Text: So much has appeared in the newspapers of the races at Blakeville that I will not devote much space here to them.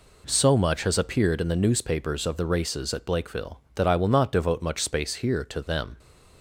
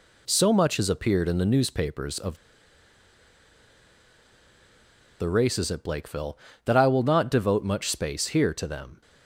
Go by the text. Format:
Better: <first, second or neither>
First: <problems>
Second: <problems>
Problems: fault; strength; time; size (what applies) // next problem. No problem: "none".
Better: first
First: none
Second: pauses between "of" and "the"; strong; at 2.3 s; 2.8 s long